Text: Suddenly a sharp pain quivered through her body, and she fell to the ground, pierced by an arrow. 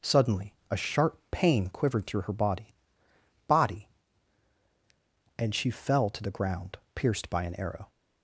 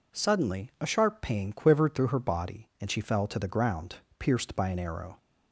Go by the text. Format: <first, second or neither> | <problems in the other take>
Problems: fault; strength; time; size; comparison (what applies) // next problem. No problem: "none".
second | says "body" twice; at 3.4 s